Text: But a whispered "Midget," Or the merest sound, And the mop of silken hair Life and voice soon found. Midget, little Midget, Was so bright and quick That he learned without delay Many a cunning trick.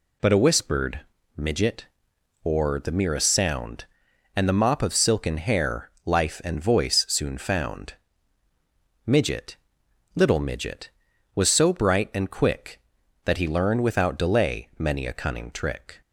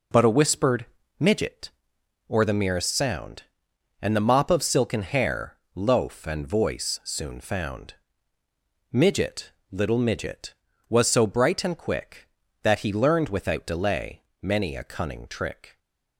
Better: first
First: pauses between "whispered" and "Midget"; slight; at 1.0 s; 0.34 s long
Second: pauses between "whispered" and "Midget"; slight; at 0.8 s; 0.34 s long // says "Loaf" for "Life"; at 5.7 s // pauses between "delay" and "Many"; slight; at 14.2 s; 0.20 s long

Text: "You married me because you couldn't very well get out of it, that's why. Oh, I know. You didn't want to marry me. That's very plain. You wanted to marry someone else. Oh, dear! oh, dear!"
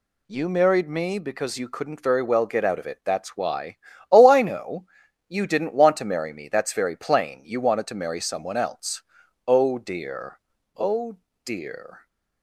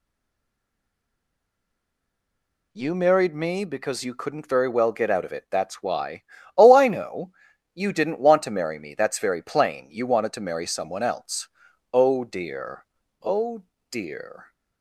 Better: first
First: none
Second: stays silent before the first word; strong; until 2.7 s; 2.7 s long

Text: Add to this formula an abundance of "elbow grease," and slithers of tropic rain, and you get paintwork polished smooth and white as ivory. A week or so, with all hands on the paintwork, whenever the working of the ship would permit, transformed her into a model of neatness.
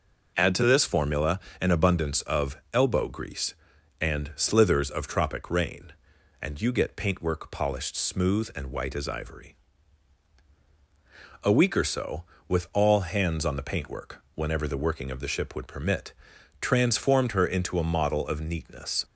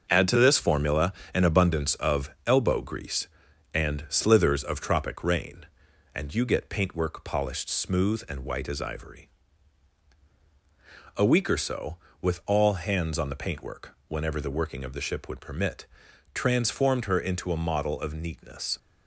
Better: first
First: pauses between "formula" and "an"; slight; at 1.3 s; 0.22 s long // pauses between "of" and "elbow"; slight; at 2.5 s; 0.16 s long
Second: gets quieter; throughout; 6.5 dB // pauses between "formula" and "an"; slight; at 1.1 s; 0.22 s long // pauses between "of" and "elbow"; slight; at 2.2 s; 0.16 s long

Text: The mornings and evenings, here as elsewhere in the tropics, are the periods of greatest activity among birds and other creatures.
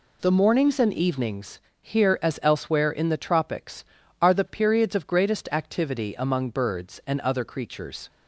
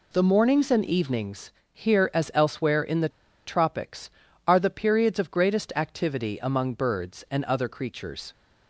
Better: first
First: none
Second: pauses between "the" and "tropics"; at 3.0 s; 0.37 s long

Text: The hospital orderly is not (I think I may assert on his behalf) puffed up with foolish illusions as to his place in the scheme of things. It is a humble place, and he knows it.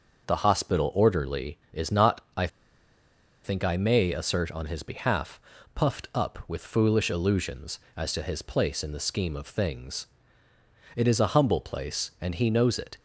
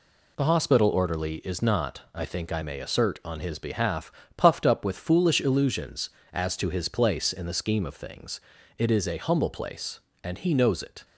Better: second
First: starts louder than the rest; until 1.3 s; 6 dB // pauses between "I" and "think"; noticeable; at 2.4 s; 0.97 s long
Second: none

